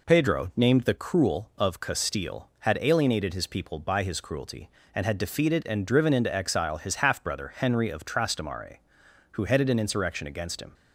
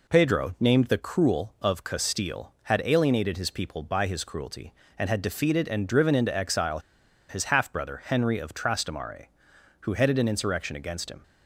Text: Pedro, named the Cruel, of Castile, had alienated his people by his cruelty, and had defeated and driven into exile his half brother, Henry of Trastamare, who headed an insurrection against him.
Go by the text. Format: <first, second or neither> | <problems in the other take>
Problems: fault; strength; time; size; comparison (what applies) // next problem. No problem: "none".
first | pauses between "exile" and "his"; noticeable; at 6.7 s; 0.49 s long